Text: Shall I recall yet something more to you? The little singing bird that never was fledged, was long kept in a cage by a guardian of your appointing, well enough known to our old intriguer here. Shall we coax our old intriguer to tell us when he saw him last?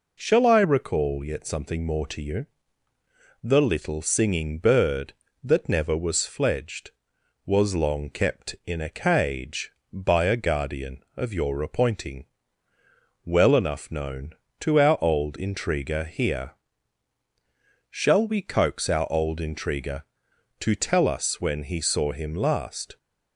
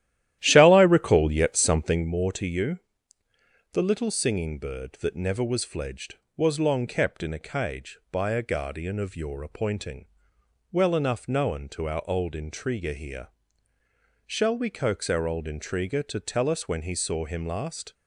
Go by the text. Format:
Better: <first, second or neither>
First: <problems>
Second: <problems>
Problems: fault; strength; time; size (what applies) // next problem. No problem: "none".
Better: first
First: none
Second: starts louder than the rest; strong; until 2.1 s; 13 dB